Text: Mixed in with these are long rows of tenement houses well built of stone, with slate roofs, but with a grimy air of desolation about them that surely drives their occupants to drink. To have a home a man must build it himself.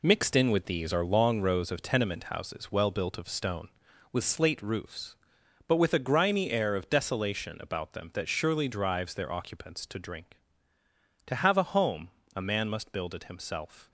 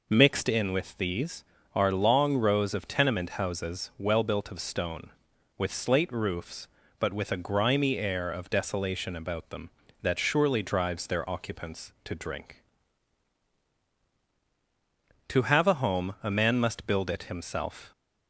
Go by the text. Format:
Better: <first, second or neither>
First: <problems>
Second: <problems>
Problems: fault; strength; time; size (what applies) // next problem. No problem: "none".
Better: second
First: gets quieter; strong; throughout; 8 dB // pauses between "home" and "a"; slight; at 12.1 s; 0.26 s long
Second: none